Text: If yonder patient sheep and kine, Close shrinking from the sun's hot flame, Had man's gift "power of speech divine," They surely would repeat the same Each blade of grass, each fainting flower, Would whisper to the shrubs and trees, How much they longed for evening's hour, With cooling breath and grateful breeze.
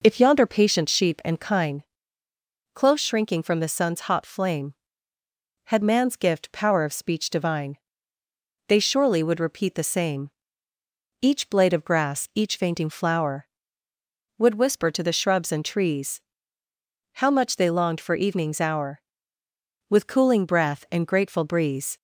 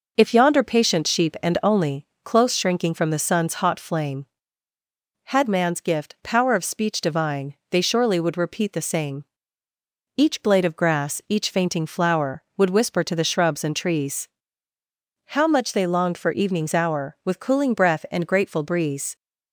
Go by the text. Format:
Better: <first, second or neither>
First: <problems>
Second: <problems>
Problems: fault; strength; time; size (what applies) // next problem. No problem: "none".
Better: first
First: pauses between "same" and "Each"; noticeable; at 10.3 s; 0.90 s long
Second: says "only" for "kine"; at 1.6 s // pauses between "same" and "Each"; noticeable; at 9.2 s; 0.94 s long